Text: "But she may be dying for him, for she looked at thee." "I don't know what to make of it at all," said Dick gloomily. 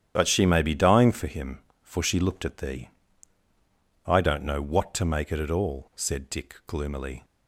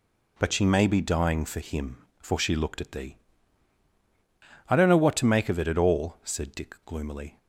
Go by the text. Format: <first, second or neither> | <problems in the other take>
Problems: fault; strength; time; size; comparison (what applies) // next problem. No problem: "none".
second | starts louder than the rest; strong; until 1.1 s; 9.5 dB // skips "of"; at 5.3 s